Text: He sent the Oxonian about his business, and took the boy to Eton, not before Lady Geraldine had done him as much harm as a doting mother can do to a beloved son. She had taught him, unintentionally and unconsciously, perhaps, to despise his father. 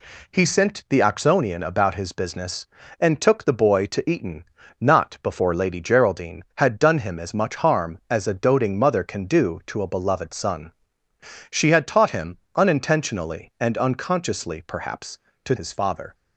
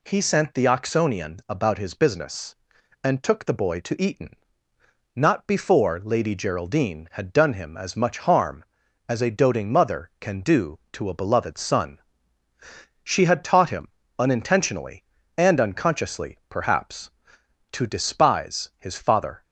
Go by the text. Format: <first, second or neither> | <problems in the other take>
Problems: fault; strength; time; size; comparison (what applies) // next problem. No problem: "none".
second | skips "despise"; at 15.5 s